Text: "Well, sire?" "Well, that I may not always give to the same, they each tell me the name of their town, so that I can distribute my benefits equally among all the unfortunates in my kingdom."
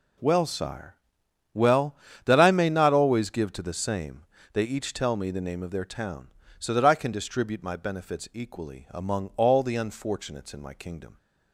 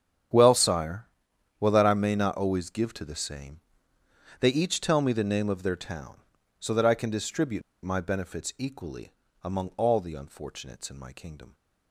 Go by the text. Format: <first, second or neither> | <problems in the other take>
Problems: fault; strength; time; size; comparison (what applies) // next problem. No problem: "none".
first | starts louder than the rest; strong; until 1.8 s; 8.5 dB // pauses between "distribute" and "my"; slight; at 7.6 s; 0.21 s long // pauses between "equally" and "among"; slight; at 9.1 s; 0.30 s long